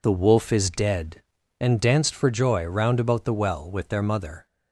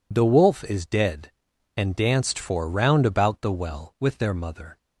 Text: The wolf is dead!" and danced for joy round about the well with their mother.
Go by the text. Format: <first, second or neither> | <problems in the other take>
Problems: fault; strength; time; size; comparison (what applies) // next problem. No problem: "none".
first | skips "joy"; at 2.6 s